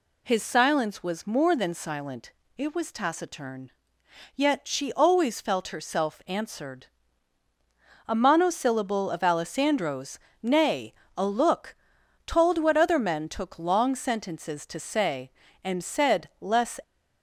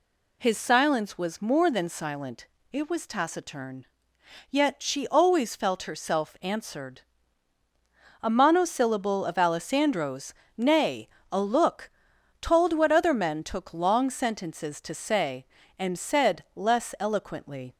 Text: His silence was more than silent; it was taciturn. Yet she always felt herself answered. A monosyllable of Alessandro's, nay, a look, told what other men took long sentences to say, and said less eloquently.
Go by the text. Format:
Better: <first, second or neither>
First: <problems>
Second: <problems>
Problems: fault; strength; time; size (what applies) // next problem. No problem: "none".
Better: second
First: stops before "eloquently"; at 16.8 s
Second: none